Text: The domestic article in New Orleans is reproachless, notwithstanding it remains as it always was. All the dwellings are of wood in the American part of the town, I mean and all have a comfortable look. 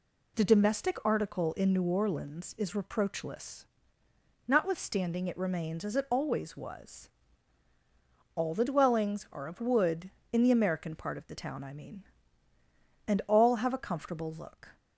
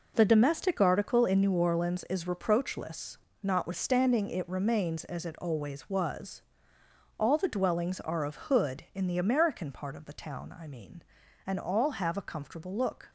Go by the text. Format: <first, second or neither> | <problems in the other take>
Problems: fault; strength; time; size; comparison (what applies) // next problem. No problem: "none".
first | says "hood" for "wood"; at 8.3 s